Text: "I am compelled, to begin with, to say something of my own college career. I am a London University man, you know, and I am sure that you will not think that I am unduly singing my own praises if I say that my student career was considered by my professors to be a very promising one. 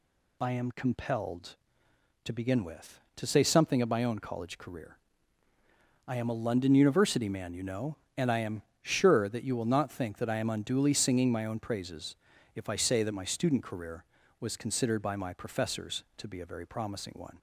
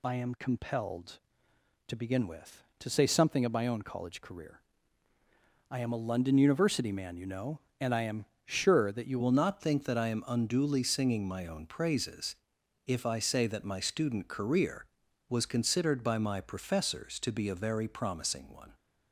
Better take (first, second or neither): first